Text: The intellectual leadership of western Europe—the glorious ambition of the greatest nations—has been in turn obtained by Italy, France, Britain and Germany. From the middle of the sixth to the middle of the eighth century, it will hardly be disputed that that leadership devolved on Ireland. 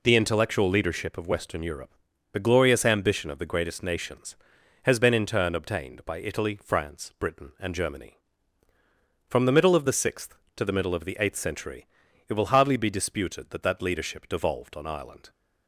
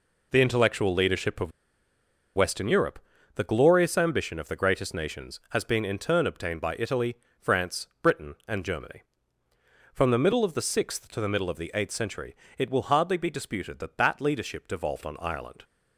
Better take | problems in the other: first | pauses between "of" and "western"; noticeable; at 1.5 s; 0.86 s long

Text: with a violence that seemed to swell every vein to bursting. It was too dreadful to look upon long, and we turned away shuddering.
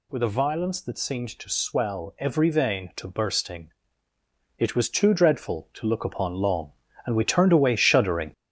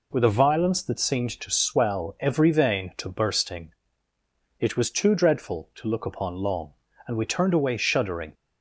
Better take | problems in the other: second | gets louder; noticeable; throughout; 6 dB

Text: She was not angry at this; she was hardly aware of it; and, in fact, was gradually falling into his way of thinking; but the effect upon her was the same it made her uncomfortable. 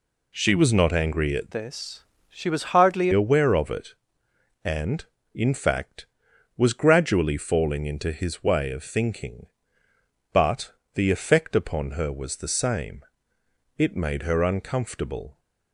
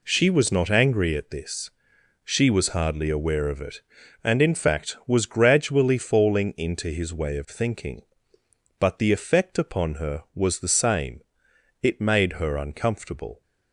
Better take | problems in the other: second | changes voice from "this" to "hardly"; from 1.5 to 3.1 s; 1.6 s long // pauses between "but" and "the"; slight; at 10.7 s; 0.22 s long // pauses between "same" and "it"; noticeable; at 13.0 s; 0.72 s long; noticeable in the second

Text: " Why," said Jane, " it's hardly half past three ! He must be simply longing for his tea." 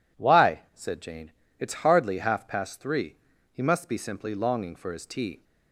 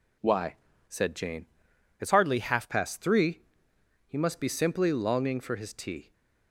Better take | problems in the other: first | changes voice from "hardly" to "half"; from 2.1 to 2.6 s; 0.5 s long

